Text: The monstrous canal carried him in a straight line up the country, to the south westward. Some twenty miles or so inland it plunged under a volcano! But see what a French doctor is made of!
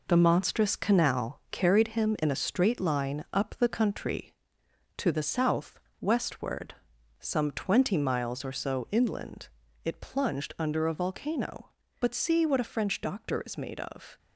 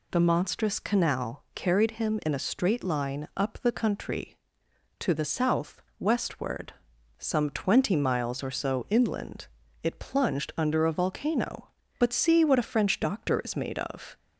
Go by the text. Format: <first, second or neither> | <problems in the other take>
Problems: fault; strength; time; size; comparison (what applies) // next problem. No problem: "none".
second | gets quieter; throughout; 6.5 dB // pauses between "south" and "westward"; slight; at 5.7 s; 0.21 s long; slight in the second // pauses between "inland" and "it"; slight; at 9.4 s; 0.36 s long; slight in the second